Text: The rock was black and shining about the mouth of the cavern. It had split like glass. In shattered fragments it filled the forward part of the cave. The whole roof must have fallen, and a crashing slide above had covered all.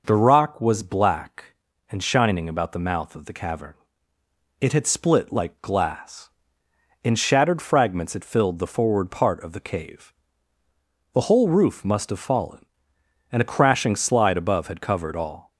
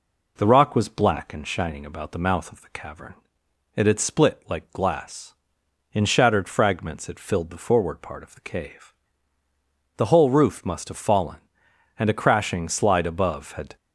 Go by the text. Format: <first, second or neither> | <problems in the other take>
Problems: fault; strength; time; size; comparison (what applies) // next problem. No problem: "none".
first | stops before "covered all"; at 13.7 s